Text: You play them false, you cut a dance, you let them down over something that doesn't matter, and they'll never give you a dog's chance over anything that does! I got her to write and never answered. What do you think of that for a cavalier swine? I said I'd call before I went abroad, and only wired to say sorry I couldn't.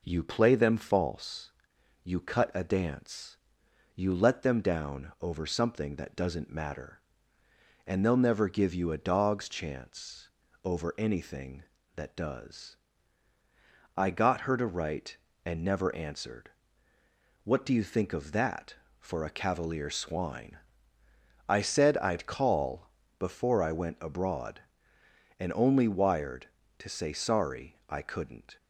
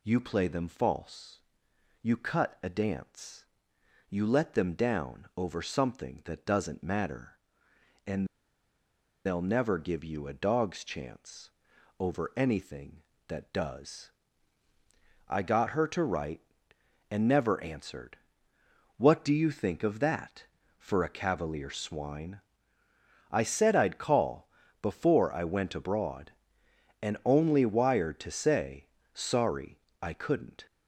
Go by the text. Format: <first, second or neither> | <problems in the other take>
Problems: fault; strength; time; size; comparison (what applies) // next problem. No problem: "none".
first | pauses between "and" and "they'll"; at 8.2 s; 1.0 s long // pauses between "chance" and "over"; noticeable; at 11.4 s; 0.50 s long; also in the first // pauses between "call" and "before"; slight; at 24.4 s; 0.34 s long; slight in the first // pauses between "say" and "sorry"; slight; at 28.8 s; 0.26 s long // pauses between "sorry" and "I"; slight; at 29.7 s; 0.24 s long